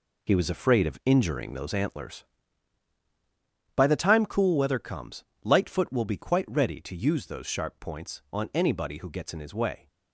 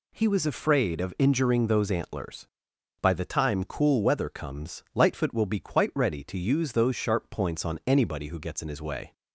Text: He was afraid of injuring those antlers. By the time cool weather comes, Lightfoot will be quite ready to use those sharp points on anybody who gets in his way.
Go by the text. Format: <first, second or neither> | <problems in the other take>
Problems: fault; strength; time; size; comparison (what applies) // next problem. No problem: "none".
second | gets quieter; strong; throughout; 8 dB